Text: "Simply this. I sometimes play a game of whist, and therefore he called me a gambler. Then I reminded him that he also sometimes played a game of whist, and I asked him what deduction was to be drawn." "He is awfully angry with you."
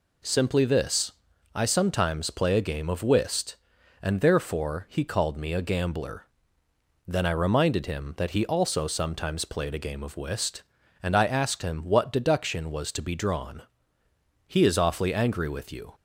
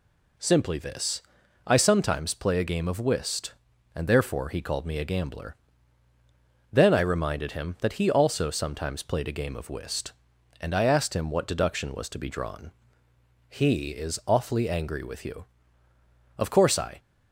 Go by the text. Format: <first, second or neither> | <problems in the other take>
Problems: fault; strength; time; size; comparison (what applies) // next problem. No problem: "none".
first | goes on to say "Of course I"; noticeable; from 16.3 s on; 0.62 s long